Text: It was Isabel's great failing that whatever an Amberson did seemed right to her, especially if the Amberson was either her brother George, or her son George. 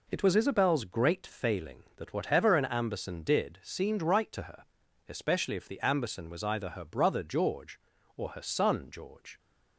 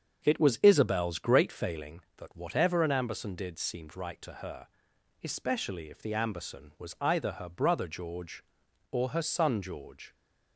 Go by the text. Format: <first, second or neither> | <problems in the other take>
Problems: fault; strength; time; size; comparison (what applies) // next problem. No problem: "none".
first | starts louder than the rest; until 2.0 s; 7 dB